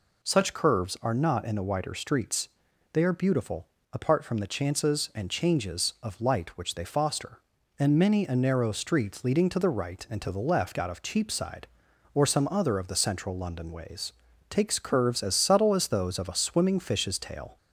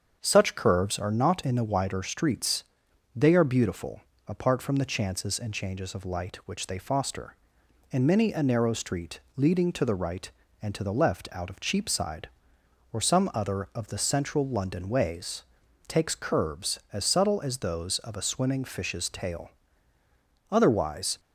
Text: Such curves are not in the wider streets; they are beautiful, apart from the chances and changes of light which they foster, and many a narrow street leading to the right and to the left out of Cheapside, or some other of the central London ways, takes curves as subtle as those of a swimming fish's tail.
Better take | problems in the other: first | starts louder than the rest; strong; until 1.2 s; 7 dB // pauses between "street" and "leading"; slight; at 9.1 s; 0.16 s long // goes on to say "Otherwise"; noticeable; from 20.4 s on; 0.70 s long

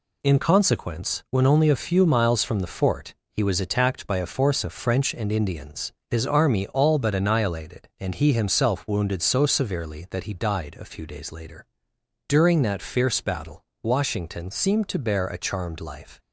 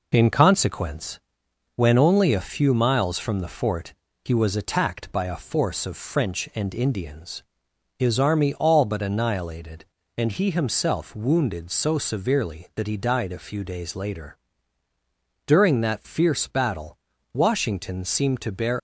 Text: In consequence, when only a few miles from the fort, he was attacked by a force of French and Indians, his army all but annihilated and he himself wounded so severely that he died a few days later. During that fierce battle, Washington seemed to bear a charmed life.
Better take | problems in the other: first | stops before "a charmed life"; at 18.7 s

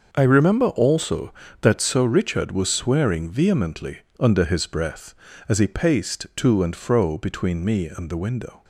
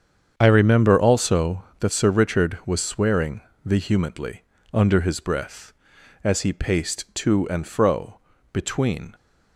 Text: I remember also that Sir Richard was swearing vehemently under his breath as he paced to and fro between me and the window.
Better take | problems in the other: first | starts louder than the rest; strong; until 1.3 s; 7.5 dB; also in the first // pauses between "swearing" and "vehemently"; slight; at 3.4 s; 0.24 s long // pauses between "vehemently" and "under"; slight; at 4.4 s; 0.30 s long; slight in the first // pauses between "fro" and "between"; slight; at 8.1 s; 0.32 s long // stops before "me and the window"; at 9.1 s

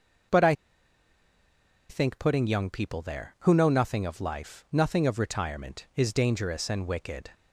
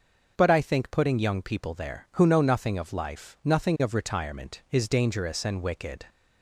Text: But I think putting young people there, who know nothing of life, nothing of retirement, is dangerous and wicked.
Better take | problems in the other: second | starts louder than the rest; noticeable; until 2.6 s; 6 dB; noticeable in the second // pauses between "I" and "think"; strong; at 0.5 s; 1.3 s long

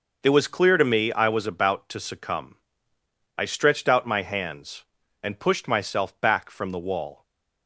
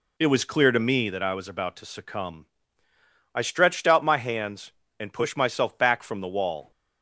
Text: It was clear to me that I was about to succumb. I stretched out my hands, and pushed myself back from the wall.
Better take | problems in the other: second | skips "that"; at 1.1 s // stays silent after the last word; slight; from 7.1 s on; 0.5 s long

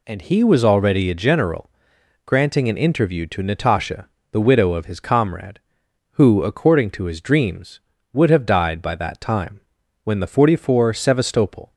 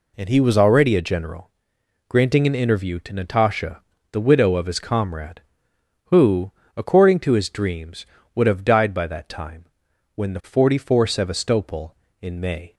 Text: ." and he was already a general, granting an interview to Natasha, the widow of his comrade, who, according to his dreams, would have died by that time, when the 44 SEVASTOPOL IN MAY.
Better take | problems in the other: second | stops before "IN MAY"; at 11.7 s

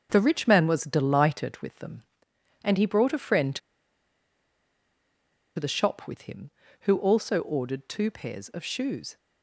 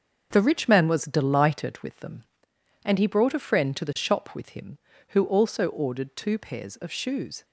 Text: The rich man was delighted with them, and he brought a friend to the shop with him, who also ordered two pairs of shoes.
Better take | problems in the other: second | starts louder than the rest; until 1.1 s; 6.5 dB; also in the second // pauses between "to" and "the"; strong; at 3.5 s; 1.9 s long

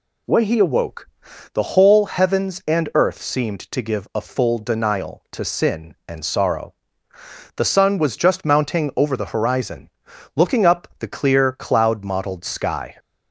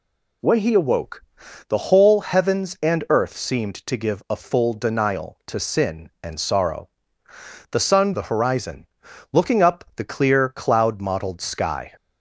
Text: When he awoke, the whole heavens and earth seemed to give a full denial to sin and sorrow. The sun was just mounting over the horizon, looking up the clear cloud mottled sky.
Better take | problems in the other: first | skips "was just mounting over"; at 8.1 s

